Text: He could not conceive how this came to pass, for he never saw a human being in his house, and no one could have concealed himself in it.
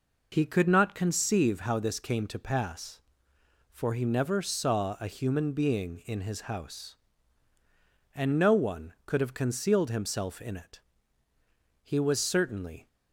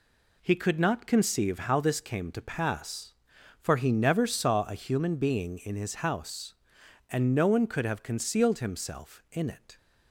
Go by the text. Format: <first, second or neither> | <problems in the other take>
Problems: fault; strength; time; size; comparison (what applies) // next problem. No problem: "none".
second | goes on to say "He was certainly"; noticeable; from 11.8 s on; 1.0 s long